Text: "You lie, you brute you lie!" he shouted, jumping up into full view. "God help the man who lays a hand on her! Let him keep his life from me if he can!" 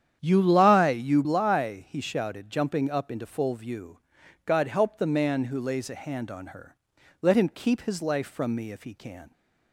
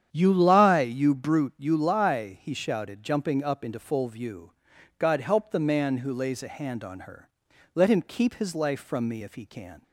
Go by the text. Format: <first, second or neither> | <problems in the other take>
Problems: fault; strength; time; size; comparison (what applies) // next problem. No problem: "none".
second | starts louder than the rest; strong; until 1.2 s; 9 dB; strong in the second // skips "brute you"; at 1.2 s